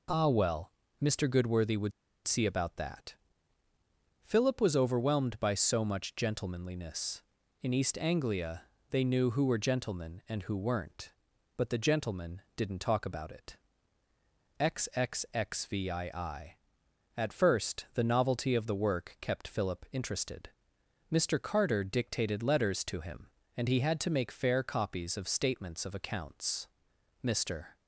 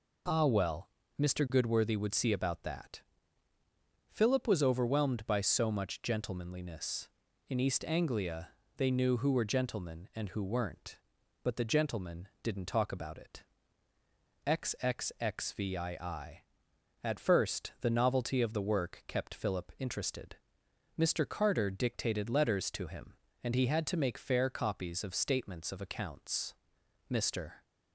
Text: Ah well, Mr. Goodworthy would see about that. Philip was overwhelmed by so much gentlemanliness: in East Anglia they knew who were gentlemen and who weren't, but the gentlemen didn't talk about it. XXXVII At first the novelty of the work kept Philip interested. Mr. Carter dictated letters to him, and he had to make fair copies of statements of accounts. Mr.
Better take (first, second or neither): second